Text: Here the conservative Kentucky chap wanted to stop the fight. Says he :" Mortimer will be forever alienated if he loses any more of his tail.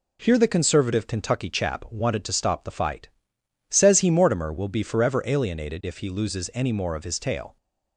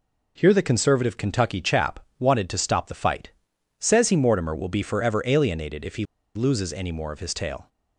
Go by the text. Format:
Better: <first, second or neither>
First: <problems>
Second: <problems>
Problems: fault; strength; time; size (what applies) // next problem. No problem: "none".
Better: first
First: none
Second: pauses between "chap" and "wanted"; slight; at 1.9 s; 0.20 s long // pauses between "he" and "loses"; slight; at 6.0 s; 0.31 s long